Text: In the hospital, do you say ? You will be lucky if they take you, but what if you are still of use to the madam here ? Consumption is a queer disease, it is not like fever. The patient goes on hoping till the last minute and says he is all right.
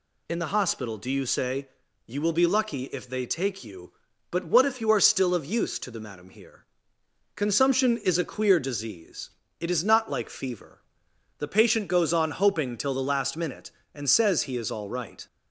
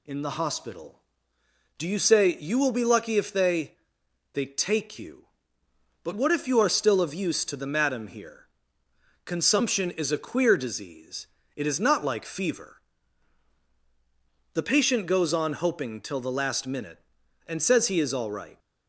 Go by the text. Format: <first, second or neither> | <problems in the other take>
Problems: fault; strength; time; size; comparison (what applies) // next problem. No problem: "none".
first | says "they" twice; at 4.3 s